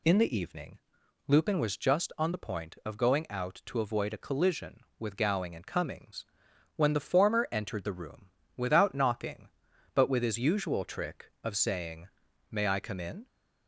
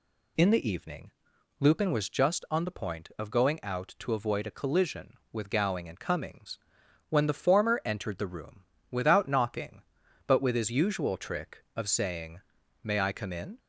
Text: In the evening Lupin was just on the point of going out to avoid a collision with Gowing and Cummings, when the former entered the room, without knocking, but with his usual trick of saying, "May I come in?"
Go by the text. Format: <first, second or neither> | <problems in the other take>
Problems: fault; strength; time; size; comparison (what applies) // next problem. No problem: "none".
neither | pauses between "evening" and "Lupin"; noticeable; the same in both